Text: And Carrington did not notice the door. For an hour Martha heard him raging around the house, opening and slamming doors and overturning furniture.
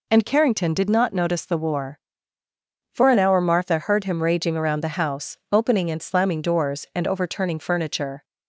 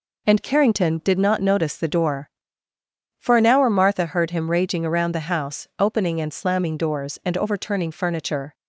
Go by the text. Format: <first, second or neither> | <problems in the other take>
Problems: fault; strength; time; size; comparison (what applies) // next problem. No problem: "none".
second | says "war" for "door"; at 1.5 s